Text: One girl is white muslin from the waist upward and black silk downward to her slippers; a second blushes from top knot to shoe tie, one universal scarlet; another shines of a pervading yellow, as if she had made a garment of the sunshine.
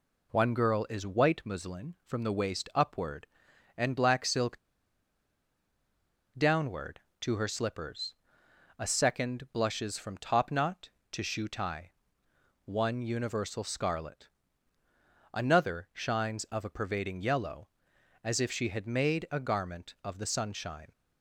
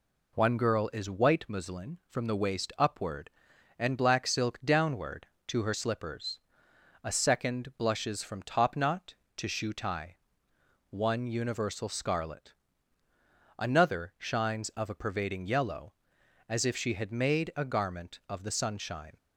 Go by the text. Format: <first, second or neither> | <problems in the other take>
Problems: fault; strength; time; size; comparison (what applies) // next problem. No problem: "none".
second | pauses between "silk" and "downward"; strong; at 4.5 s; 1.8 s long